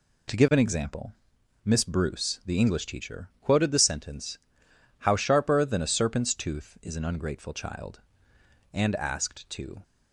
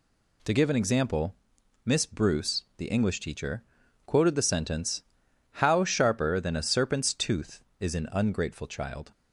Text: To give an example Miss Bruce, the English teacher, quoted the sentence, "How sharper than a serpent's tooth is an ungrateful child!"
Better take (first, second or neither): second